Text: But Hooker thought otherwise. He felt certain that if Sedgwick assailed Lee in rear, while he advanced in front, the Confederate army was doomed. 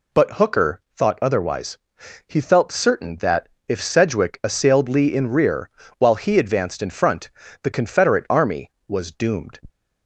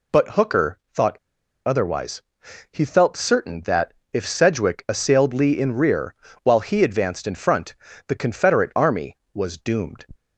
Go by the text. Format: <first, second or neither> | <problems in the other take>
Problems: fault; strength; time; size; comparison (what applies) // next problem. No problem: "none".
first | pauses between "thought" and "otherwise"; noticeable; at 1.1 s; 0.50 s long // pauses between "that" and "if"; slight; at 3.9 s; 0.22 s long; slight in the first